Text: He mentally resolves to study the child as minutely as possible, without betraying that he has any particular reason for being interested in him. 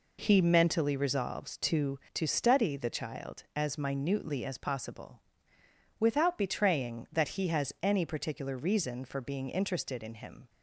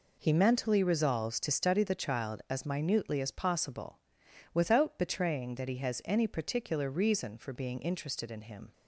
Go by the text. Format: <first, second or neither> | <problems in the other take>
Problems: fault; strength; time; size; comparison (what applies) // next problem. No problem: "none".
second | says "to" twice; at 2.1 s